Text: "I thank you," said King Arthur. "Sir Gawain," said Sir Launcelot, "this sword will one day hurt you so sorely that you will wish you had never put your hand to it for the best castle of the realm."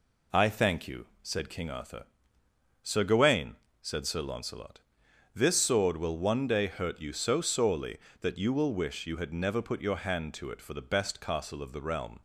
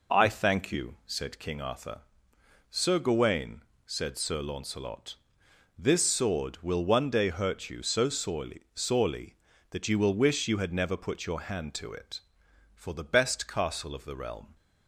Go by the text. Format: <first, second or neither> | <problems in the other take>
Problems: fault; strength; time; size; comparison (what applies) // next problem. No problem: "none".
first | says "sorely" twice; at 8.7 s